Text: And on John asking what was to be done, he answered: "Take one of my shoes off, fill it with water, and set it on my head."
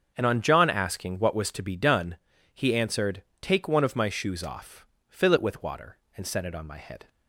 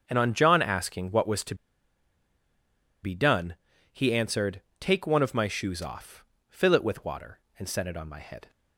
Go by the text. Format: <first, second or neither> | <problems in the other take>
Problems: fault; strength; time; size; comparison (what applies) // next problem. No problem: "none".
first | starts louder than the rest; until 1.0 s; 7 dB; also in the first // pauses between "to" and "be"; strong; at 1.5 s; 1.4 s long